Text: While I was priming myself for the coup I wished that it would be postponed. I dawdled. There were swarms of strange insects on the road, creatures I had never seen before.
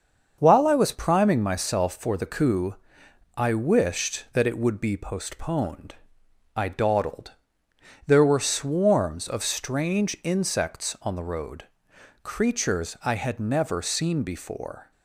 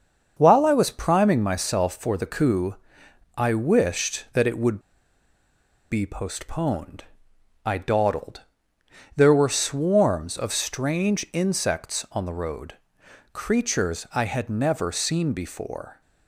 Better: first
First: starts louder than the rest; until 1.3 s; 6.5 dB // pauses between "coup" and "I"; noticeable; at 2.7 s; 0.60 s long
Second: starts louder than the rest; until 1.3 s; 6.5 dB // pauses between "coup" and "I"; noticeable; at 2.7 s; 0.60 s long // pauses between "would" and "be"; at 4.7 s; 1.1 s long

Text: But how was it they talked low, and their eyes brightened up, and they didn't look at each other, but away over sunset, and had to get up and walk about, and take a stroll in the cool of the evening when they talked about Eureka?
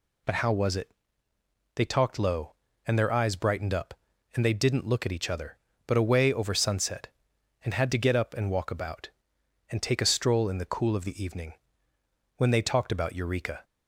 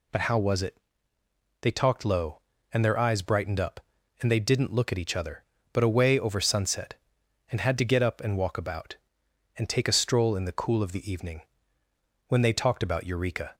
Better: neither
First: pauses between "it" and "they"; noticeable; at 0.9 s; 0.84 s long // pauses between "evening" and "when"; noticeable; at 11.5 s; 0.82 s long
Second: pauses between "it" and "they"; noticeable; at 0.7 s; 0.84 s long // pauses between "evening" and "when"; noticeable; at 11.4 s; 0.85 s long

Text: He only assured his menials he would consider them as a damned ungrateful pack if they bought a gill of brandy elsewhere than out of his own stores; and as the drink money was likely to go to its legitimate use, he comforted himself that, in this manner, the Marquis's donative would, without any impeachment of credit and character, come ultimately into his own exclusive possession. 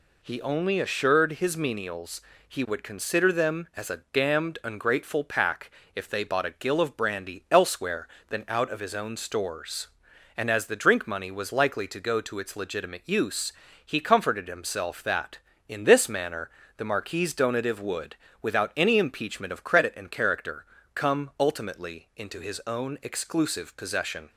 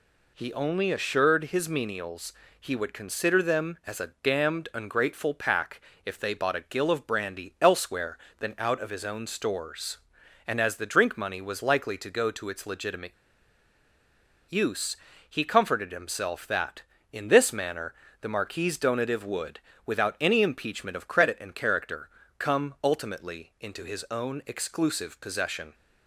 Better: first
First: pauses between "menials" and "he"; slight; at 2.2 s; 0.26 s long // pauses between "pack" and "if"; slight; at 5.7 s; 0.24 s long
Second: pauses between "menials" and "he"; slight; at 2.3 s; 0.26 s long // pauses between "pack" and "if"; slight; at 5.8 s; 0.24 s long // pauses between "legitimate" and "use"; strong; at 13.1 s; 1.3 s long

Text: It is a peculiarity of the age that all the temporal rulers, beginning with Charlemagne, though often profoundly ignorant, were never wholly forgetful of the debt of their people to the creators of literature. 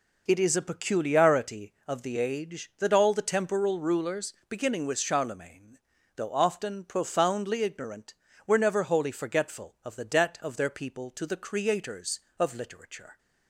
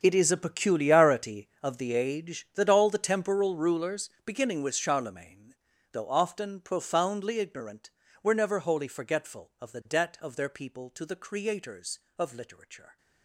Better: first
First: none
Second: gets quieter; strong; throughout; 16 dB

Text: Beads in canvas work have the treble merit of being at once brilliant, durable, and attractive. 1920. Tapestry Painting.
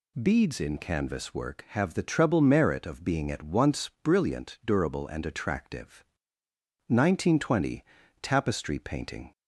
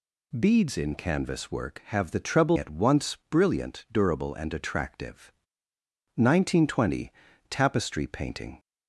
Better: first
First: none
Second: skips "merit of being"; at 2.5 s

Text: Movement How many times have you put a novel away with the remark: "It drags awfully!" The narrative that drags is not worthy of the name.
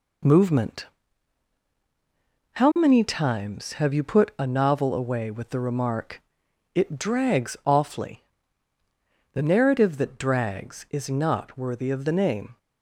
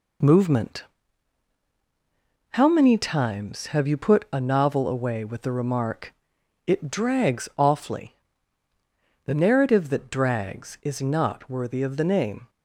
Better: neither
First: pauses between "Movement" and "How"; strong; at 0.8 s; 1.6 s long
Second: pauses between "Movement" and "How"; strong; at 0.8 s; 1.6 s long

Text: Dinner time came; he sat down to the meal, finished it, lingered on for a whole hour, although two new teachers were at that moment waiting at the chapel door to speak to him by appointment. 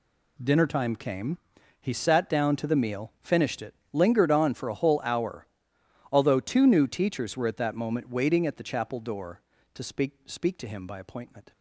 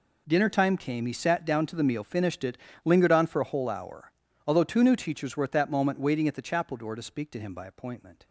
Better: second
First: says "speak" twice; at 10.2 s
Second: none

